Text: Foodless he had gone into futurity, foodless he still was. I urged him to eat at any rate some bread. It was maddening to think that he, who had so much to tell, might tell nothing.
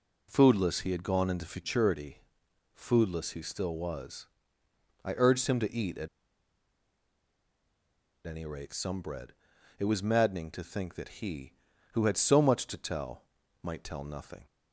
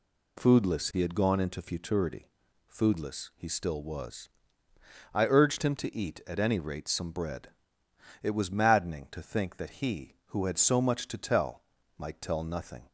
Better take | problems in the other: second | pauses between "at" and "any"; strong; at 6.0 s; 2.1 s long

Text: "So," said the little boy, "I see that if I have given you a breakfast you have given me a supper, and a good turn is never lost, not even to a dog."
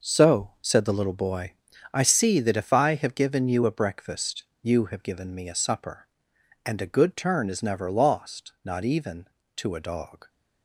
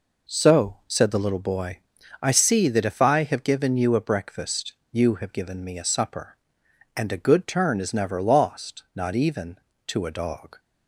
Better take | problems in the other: second | gets quieter; strong; throughout; 10.5 dB // pauses between "breakfast" and "you"; slight; at 4.4 s; 0.18 s long; slight in the second

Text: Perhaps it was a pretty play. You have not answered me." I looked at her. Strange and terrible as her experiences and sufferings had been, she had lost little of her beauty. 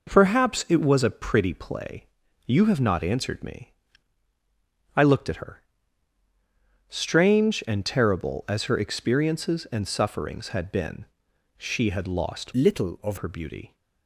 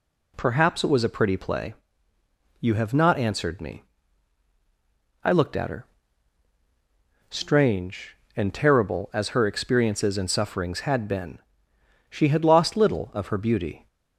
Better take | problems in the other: second | changes voice from "little" to "of"; from 12.5 to 13.1 s; 0.6 s long

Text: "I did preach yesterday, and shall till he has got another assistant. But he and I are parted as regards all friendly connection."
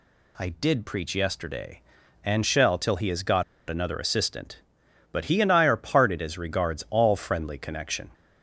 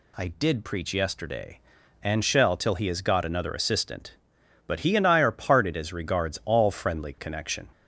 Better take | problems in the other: second | pauses between "got" and "another"; slight; at 3.4 s; 0.25 s long

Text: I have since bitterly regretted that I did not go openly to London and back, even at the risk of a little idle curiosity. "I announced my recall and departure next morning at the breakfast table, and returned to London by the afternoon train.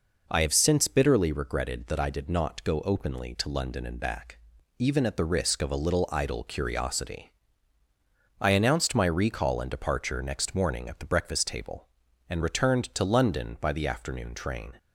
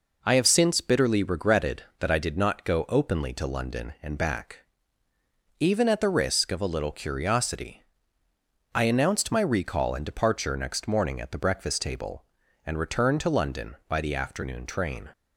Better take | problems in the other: first | skips "idle"; at 6.9 s

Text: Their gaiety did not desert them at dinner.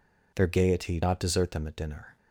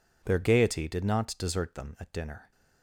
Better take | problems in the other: second | skips "did"; at 1.0 s

